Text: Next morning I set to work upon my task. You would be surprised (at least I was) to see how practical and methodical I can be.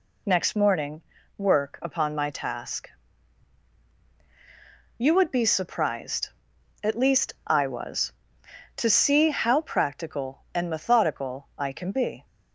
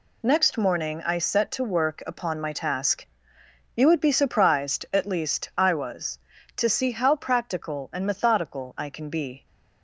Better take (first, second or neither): second